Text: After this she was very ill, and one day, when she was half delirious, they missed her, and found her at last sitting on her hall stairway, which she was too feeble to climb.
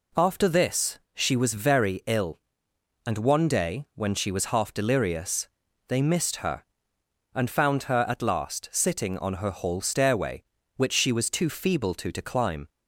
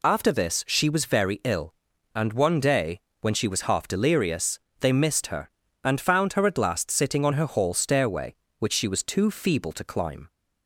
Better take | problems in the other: second | pauses between "this" and "she"; slight; at 0.9 s; 0.16 s long // says "to" twice; at 12.1 s

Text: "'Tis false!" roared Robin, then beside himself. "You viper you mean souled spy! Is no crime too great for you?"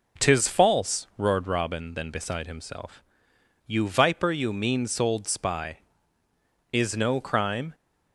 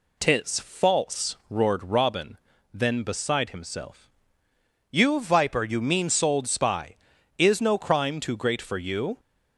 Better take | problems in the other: second | stops before "too great for you"; at 7.7 s

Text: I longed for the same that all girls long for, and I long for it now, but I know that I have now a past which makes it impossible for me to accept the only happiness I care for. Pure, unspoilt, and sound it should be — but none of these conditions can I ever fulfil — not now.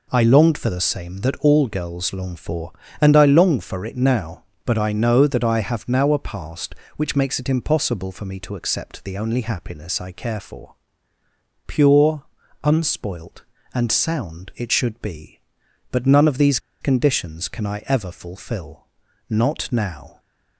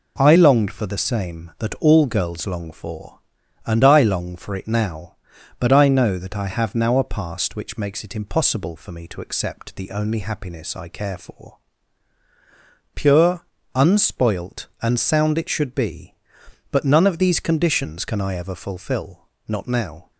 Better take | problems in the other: second | pauses between "these" and "conditions"; slight; at 16.5 s; 0.22 s long

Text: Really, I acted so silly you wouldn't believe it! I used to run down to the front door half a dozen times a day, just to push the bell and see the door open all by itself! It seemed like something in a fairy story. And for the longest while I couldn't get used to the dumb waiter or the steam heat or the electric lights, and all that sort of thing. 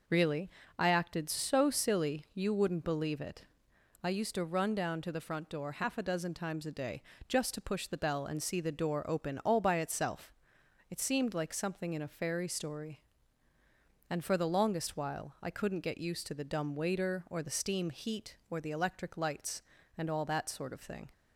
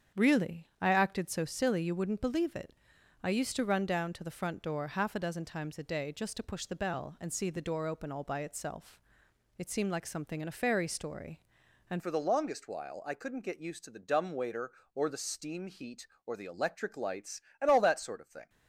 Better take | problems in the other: first | starts louder than the rest; strong; until 1.2 s; 8 dB // changes voice at "for"; from 11.9 s on; 6.5 s long

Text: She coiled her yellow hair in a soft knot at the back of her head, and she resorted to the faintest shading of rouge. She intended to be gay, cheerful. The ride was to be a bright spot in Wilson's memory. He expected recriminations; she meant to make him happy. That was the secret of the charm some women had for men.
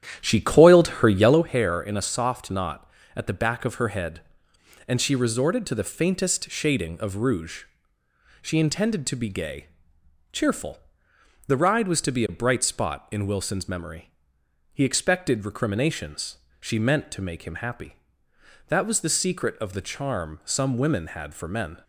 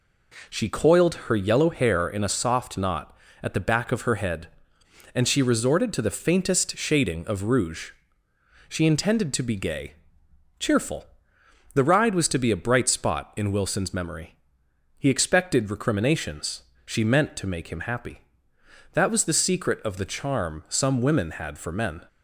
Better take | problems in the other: second | starts louder than the rest; strong; until 1.5 s; 10 dB

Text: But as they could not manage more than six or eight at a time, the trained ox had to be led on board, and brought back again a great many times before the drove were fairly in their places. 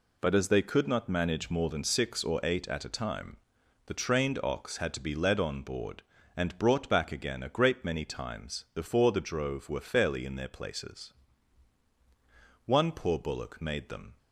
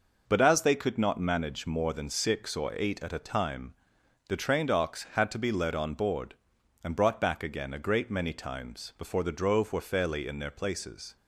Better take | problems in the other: second | goes on to say "One poor bullock made them"; from 12.6 s on; 1.5 s long

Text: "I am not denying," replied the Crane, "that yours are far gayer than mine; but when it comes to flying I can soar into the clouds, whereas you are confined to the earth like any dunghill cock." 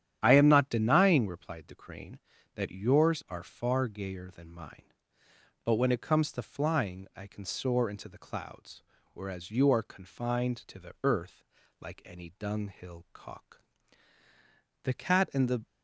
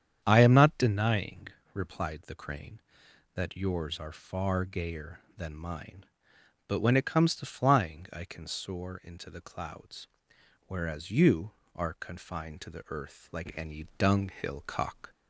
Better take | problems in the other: second | starts louder than the rest; strong; until 1.2 s; 10 dB; strong in the second // pauses between "earth" and "like"; slight; at 11.4 s; 0.36 s long // goes on to say "THE CAT AND THE"; noticeable; from 14.8 s on; 0.80 s long

